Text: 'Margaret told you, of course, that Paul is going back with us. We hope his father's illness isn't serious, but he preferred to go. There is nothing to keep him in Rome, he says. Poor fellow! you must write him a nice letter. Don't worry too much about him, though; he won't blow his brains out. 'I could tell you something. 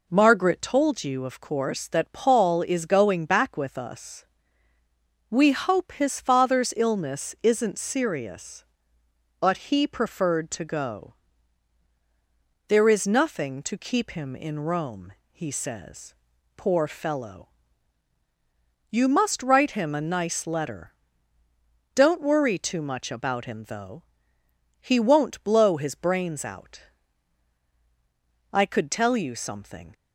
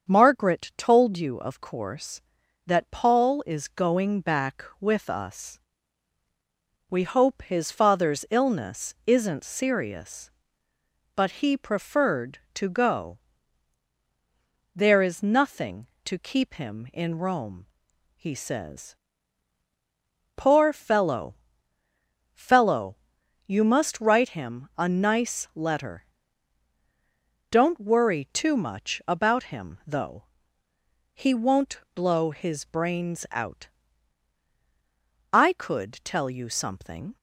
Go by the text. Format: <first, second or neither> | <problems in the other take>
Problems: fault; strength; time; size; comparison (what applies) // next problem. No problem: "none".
first | starts louder than the rest; strong; until 1.1 s; 7 dB // says "fellow" twice; at 22.3 s